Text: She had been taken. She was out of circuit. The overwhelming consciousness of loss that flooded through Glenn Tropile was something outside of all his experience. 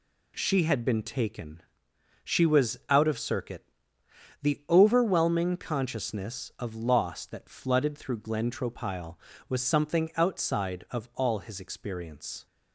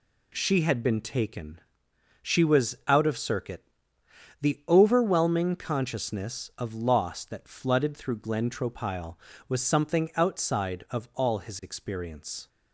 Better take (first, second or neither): neither